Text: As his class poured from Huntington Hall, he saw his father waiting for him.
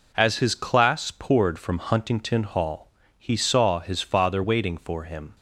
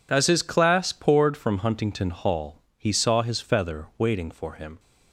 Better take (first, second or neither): first